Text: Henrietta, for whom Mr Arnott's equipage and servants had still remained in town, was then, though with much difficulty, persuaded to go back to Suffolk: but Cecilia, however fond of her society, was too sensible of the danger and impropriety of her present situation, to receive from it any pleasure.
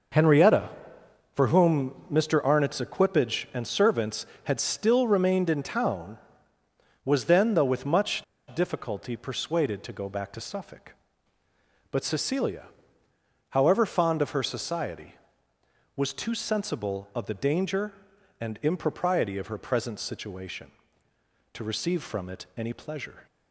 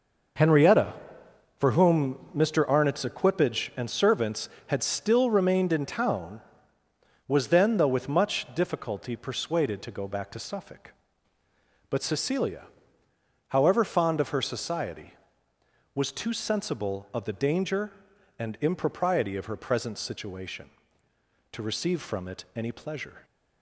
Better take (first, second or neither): second